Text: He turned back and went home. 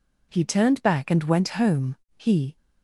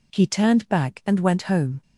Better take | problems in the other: second | goes on to say "He"; slight; from 2.1 s on; 0.38 s long

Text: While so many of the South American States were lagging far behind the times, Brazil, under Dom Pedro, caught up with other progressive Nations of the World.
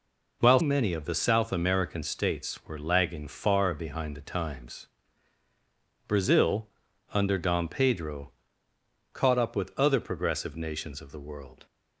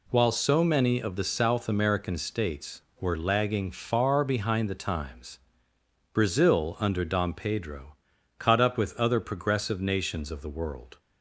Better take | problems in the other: second | skips "so"; at 0.5 s

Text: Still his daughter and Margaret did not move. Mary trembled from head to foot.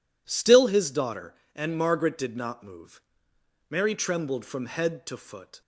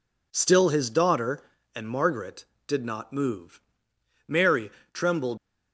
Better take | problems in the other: first | pauses between "Mary" and "trembled"; slight; at 4.7 s; 0.22 s long // stops before "from head to foot"; at 5.3 s

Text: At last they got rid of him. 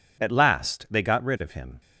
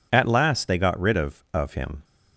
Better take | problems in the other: first | says "of" twice; at 1.5 s

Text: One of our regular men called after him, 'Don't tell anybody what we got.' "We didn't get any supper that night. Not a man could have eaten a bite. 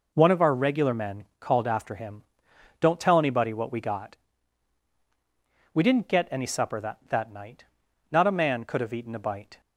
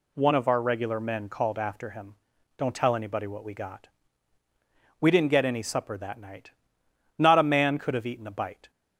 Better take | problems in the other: second | pauses between "men" and "called"; slight; at 1.2 s; 0.16 s long // says "that" twice; at 7.0 s

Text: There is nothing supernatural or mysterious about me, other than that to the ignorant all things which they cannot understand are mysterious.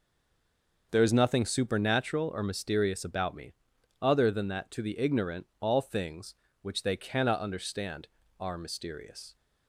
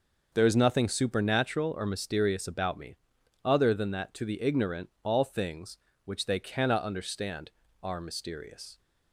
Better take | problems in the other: second | stays silent before the first word; slight; until 0.9 s; 0.9 s long

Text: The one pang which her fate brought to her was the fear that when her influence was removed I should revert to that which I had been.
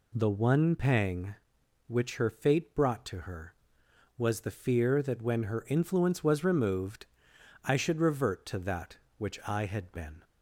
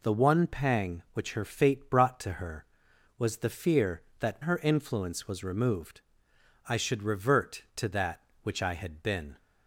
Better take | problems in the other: first | skips "when"; at 4.4 s // pauses between "removed" and "I"; noticeable; at 6.0 s; 0.66 s long; noticeable in the first

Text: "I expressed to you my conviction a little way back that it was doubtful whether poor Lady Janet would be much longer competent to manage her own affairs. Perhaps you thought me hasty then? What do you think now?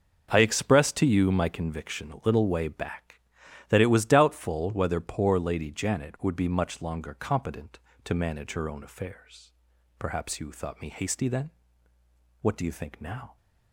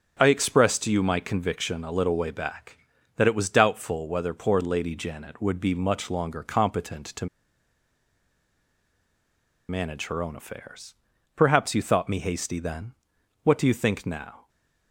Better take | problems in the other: first | starts louder than the rest; until 1.2 s; 7 dB; also in the first // pauses between "to" and "manage"; strong; at 7.2 s; 2.4 s long // stays silent after the last word; slight; from 14.4 s on; 0.5 s long

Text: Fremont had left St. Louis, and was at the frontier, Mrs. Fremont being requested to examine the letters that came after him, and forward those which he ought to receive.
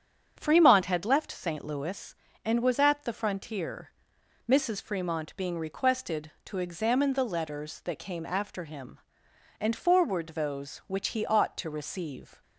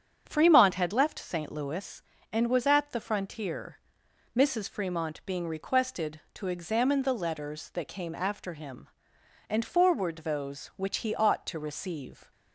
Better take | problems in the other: neither | starts louder than the rest; strong; the same in both

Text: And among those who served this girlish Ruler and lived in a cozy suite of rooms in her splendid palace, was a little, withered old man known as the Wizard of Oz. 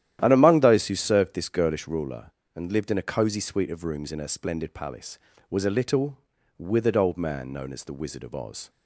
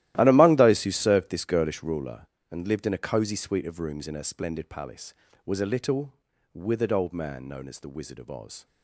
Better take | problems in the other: first | gets quieter; strong; throughout; 15.5 dB // starts louder than the rest; strong; until 1.1 s; 14.5 dB; strong in the first

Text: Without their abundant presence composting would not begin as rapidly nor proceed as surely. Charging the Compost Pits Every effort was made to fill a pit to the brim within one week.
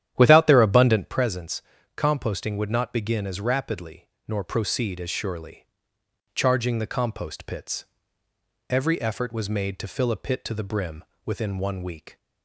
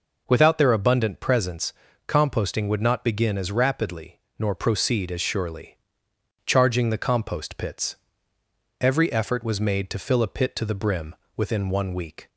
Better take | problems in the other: second | starts louder than the rest; strong; until 1.2 s; 11 dB // pauses between "presence" and "composting"; slight; at 1.6 s; 0.36 s long; slight in the second // pauses between "rapidly" and "nor"; slight; at 4.0 s; 0.20 s long; slight in the second // pauses between "Pits" and "Every"; noticeable; at 7.8 s; 0.84 s long; noticeable in the second // pauses between "brim" and "within"; slight; at 11.0 s; 0.22 s long; slight in the second

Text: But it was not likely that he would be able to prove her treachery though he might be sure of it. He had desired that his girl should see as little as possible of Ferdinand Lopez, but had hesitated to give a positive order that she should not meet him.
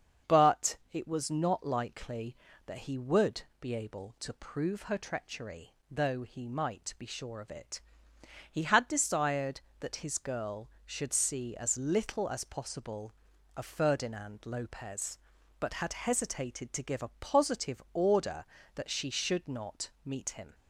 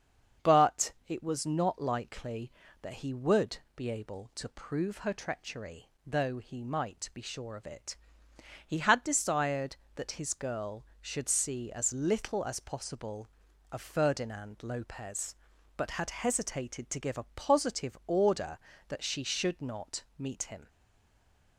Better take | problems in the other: first | starts louder than the rest; until 1.5 s; 7 dB; also in the first // pauses between "But" and "it"; slight; at 0.9 s; 0.16 s long; slight in the first // pauses between "would" and "be"; slight; at 3.5 s; 0.18 s long; slight in the first // pauses between "treachery" and "though"; slight; at 5.8 s; 0.20 s long; slight in the first // stays silent after the last word; slight; from 20.6 s on; 0.9 s long

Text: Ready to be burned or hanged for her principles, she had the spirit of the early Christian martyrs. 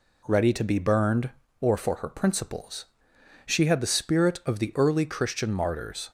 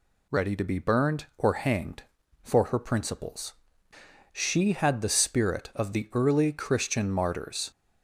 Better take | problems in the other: second | skips "hanged"; at 1.7 s

